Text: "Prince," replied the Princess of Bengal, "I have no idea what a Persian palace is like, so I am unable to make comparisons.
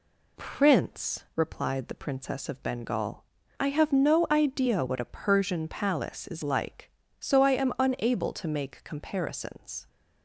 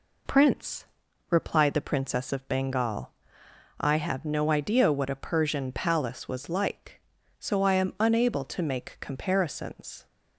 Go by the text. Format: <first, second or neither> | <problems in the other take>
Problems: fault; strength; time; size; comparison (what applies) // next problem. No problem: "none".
first | says "was" for "is"; at 6.2 s